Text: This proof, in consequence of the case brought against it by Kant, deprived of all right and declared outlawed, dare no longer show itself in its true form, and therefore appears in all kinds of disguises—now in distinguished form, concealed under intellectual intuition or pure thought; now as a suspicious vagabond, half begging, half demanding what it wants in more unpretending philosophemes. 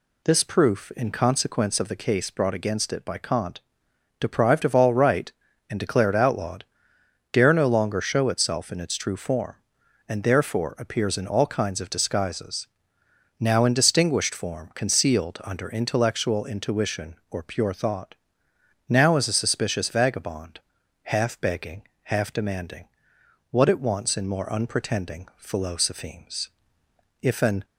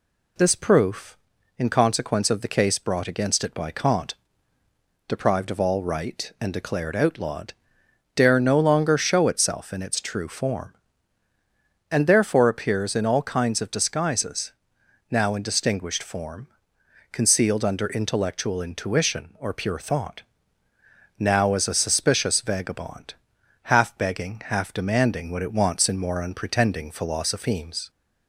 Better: second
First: pauses between "demanding" and "what"; noticeable; at 22.8 s; 0.62 s long // goes on to say "If an"; slight; from 27.2 s on; 0.42 s long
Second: none

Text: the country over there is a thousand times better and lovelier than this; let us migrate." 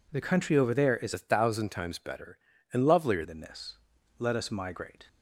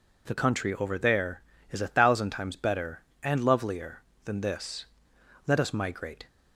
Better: second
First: changes voice from "a" to "lovelier"; from 1.1 to 3.2 s; 2.1 s long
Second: none

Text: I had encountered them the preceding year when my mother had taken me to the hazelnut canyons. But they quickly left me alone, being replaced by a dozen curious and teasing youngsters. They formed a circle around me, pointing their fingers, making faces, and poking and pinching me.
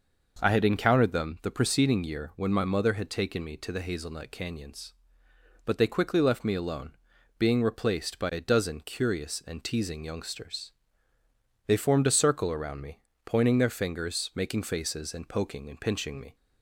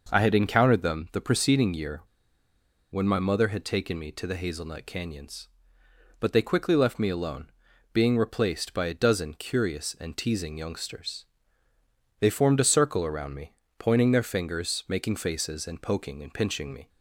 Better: first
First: none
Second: pauses between "year" and "when"; noticeable; at 2.0 s; 0.90 s long

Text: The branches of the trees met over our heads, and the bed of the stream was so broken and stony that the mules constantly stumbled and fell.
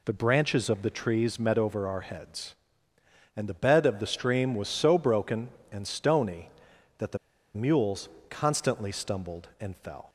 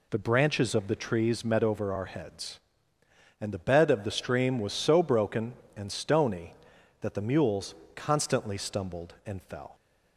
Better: second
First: pauses between "the" and "mules"; at 7.1 s; 0.37 s long // pauses between "mules" and "constantly"; slight; at 8.0 s; 0.22 s long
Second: pauses between "mules" and "constantly"; slight; at 7.7 s; 0.22 s long

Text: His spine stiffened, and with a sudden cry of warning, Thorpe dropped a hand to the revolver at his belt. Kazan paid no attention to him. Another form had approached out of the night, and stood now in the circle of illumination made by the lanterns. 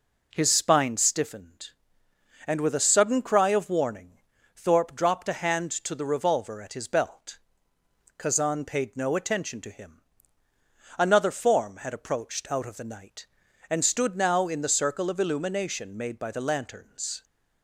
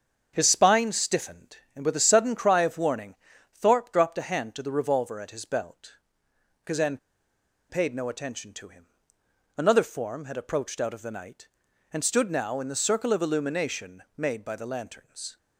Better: first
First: none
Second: starts louder than the rest; strong; until 1.3 s; 7 dB // pauses between "Kazan" and "paid"; noticeable; at 6.9 s; 0.73 s long // pauses between "illumination" and "made"; slight; at 14.0 s; 0.16 s long

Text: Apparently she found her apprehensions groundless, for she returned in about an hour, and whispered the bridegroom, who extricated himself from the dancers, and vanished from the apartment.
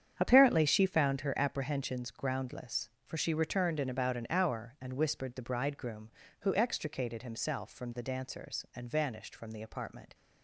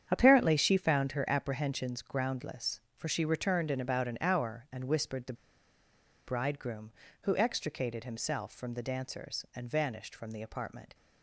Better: first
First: starts louder than the rest; strong; until 1.2 s; 8.5 dB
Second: starts louder than the rest; strong; until 1.1 s; 8.5 dB // pauses between "the" and "bridegroom"; noticeable; at 5.3 s; 0.93 s long

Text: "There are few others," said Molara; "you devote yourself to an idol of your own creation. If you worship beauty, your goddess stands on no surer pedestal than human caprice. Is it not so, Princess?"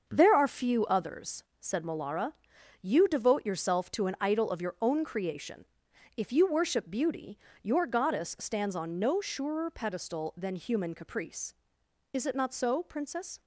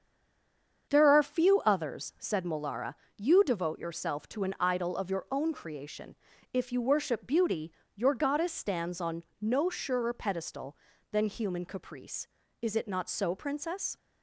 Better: first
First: starts louder than the rest; until 1.0 s; 6.5 dB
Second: stays silent before the first word; slight; until 0.8 s; 0.8 s long // starts louder than the rest; strong; until 1.9 s; 7 dB // pauses between "on" and "no"; slight; at 9.2 s; 0.16 s long

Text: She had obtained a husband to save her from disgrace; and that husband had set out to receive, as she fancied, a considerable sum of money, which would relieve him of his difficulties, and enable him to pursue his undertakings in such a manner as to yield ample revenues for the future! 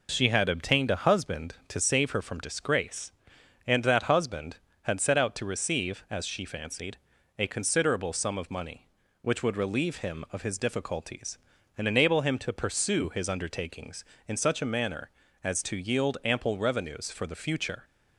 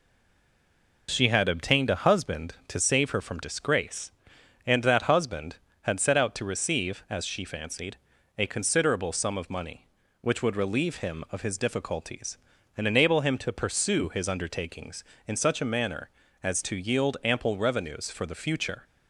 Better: first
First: none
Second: stays silent before the first word; until 1.0 s; 1.0 s long

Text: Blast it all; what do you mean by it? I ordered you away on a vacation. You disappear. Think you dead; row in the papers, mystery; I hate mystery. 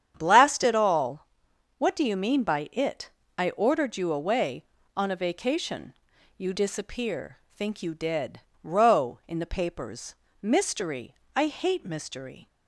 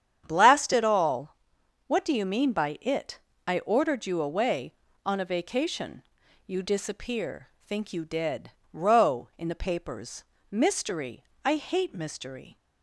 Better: neither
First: starts louder than the rest; strong; until 1.1 s; 9 dB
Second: starts louder than the rest; strong; until 1.2 s; 9 dB

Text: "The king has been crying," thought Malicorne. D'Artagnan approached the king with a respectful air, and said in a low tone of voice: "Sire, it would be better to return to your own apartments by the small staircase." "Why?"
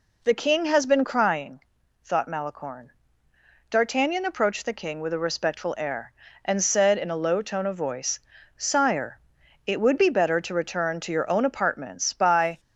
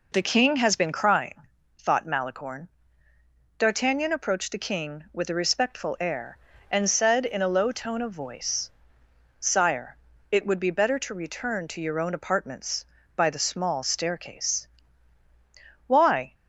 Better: second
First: stops before "the small staircase Why"; at 12.5 s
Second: none

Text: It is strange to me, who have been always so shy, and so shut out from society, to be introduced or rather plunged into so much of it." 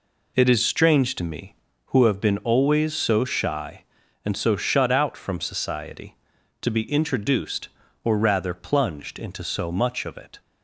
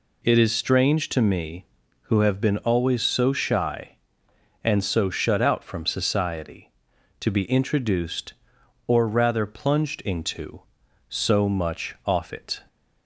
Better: first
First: none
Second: says "off" for "of"; at 12.0 s

